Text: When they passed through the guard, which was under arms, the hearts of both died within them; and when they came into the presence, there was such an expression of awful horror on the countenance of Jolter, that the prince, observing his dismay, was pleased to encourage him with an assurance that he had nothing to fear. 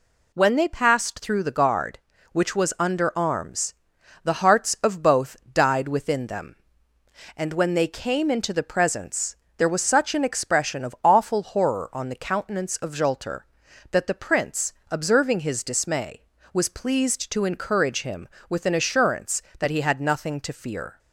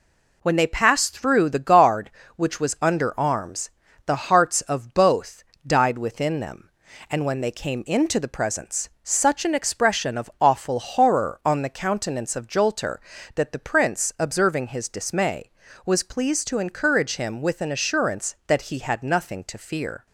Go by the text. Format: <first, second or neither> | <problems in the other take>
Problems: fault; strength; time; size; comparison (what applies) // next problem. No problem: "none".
first | pauses between "both" and "died"; slight; at 5.4 s; 0.24 s long; slight in the first // skips "there was"; at 8.9 s